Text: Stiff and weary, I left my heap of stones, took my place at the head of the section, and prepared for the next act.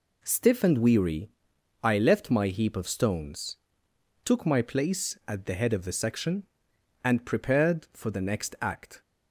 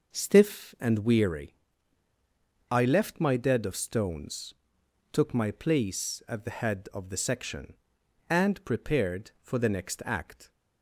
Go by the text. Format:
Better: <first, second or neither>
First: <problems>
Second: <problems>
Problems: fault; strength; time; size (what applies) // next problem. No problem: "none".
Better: first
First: none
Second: says "dead" for "heap"; at 3.3 s